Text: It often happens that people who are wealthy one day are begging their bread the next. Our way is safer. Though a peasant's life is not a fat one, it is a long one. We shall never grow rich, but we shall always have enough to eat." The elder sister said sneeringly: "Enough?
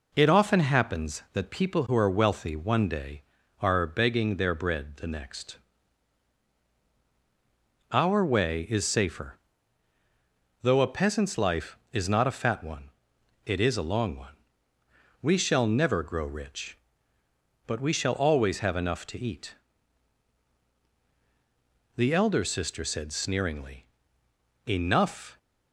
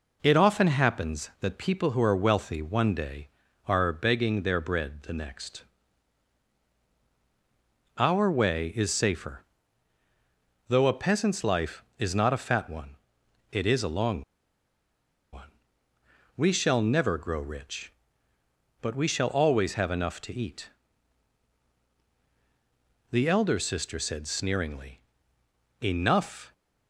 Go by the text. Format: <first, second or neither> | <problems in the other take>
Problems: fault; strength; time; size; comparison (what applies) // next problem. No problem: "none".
first | pauses between "long" and "one"; at 14.2 s; 1.1 s long